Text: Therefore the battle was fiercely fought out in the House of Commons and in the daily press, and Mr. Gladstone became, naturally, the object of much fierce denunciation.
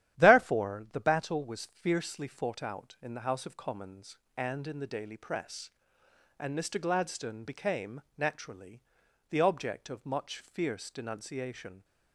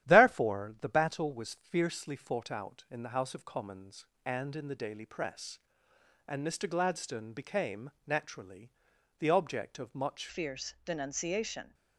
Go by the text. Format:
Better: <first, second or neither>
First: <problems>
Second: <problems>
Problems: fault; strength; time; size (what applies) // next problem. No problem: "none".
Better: first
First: starts louder than the rest; strong; until 1.2 s; 11.5 dB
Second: starts louder than the rest; strong; until 1.1 s; 11.5 dB // changes voice at "fierce"; from 10.2 s on; 1.5 s long